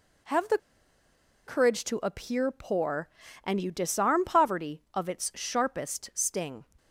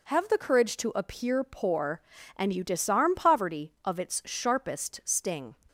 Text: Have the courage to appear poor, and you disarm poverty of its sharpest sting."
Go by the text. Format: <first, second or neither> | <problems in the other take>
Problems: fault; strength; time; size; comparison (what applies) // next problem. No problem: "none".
second | pauses between "the" and "courage"; noticeable; at 0.5 s; 0.89 s long